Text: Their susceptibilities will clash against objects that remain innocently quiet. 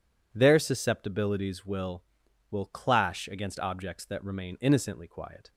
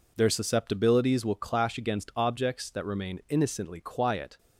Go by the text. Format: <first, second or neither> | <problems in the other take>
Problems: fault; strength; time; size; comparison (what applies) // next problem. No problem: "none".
second | says "will" twice; at 2.5 s